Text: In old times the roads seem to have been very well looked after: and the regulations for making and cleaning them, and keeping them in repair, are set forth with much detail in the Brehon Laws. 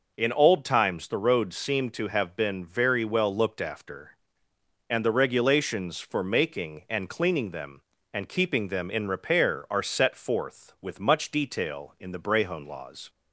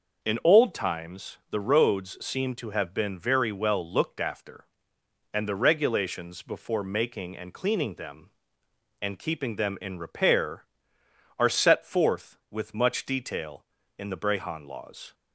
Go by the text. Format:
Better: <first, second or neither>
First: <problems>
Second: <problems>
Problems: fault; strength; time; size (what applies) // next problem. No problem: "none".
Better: first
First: none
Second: starts louder than the rest; noticeable; until 1.3 s; 6 dB // says "before" for "for"; at 6.4 s